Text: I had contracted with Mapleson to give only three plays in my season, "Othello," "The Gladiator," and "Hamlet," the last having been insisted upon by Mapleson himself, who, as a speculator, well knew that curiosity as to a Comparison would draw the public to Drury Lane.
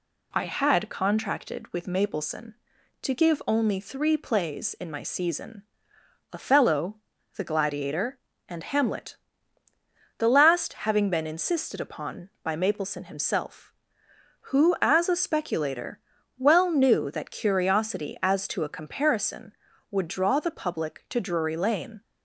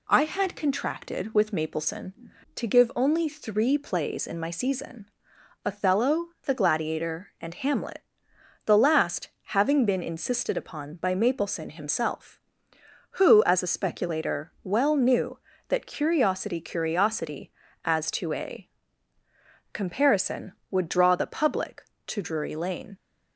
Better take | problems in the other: first | pauses between "last" and "having"; slight; at 9.2 s; 0.20 s long // says "curiosity" twice; at 16.6 s // pauses between "a" and "Comparison"; at 18.6 s; 1.0 s long

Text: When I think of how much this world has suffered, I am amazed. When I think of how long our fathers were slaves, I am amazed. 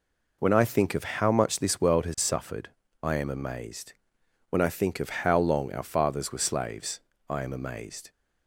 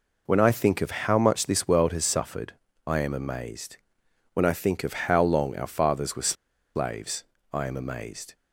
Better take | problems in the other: first | pauses between "were" and "slaves"; at 6.3 s; 0.41 s long

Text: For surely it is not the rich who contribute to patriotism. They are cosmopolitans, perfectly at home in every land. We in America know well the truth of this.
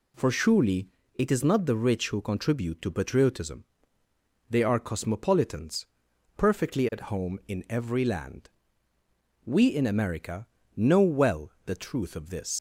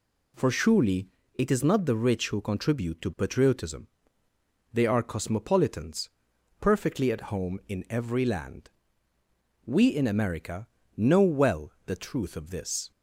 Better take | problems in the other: second | pauses between "surely" and "it"; slight; at 0.8 s; 0.28 s long; slight in the second // pauses between "America" and "know"; slight; at 10.4 s; 0.30 s long; slight in the second // leaves "this" unfinished; at 12.5 s; 110 ms

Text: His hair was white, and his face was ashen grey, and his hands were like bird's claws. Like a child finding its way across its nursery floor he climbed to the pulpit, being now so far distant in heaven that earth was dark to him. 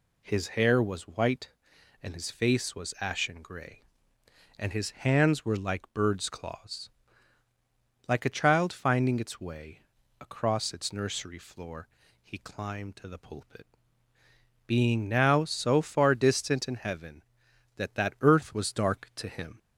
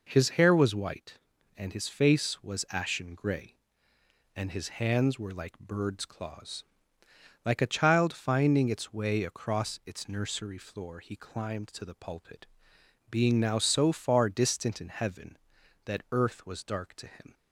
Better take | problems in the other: second | pauses between "way" and "across"; at 9.7 s; 0.40 s long // pauses between "floor" and "he"; slight; at 11.8 s; 0.34 s long // says "that" twice; at 17.9 s

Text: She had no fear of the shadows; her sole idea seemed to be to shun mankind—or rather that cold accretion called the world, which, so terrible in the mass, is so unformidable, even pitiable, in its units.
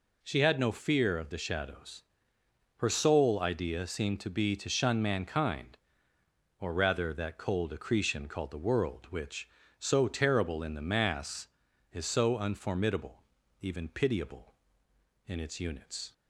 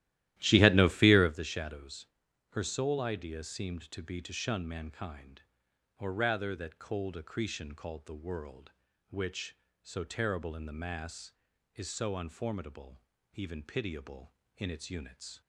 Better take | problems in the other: first | starts louder than the rest; strong; until 1.4 s; 14.5 dB

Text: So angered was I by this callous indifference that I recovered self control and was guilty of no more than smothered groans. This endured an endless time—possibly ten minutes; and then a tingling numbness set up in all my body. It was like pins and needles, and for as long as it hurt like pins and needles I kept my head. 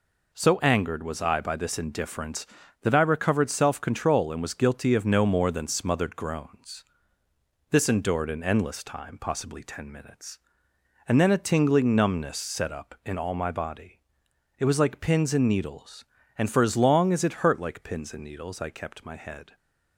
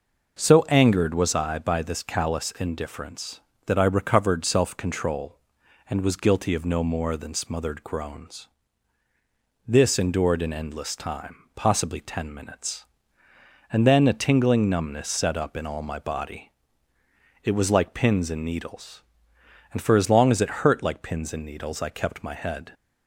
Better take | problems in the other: second | skips "callous"; at 1.7 s

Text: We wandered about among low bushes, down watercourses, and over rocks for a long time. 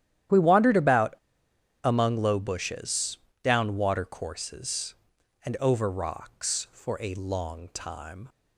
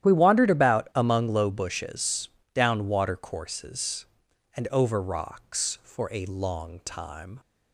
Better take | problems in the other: second | starts louder than the rest; strong; until 2.0 s; 11.5 dB; strong in the second // pauses between "about" and "among"; noticeable; at 1.1 s; 0.70 s long

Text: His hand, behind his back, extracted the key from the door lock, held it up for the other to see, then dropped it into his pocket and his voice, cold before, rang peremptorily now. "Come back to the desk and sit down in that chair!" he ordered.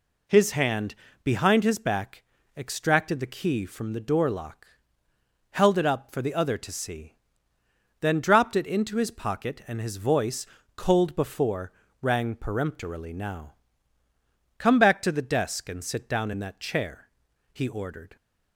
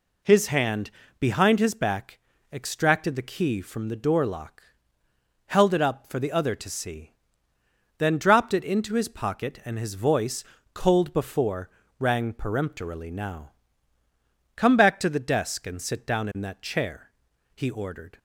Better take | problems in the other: neither | none

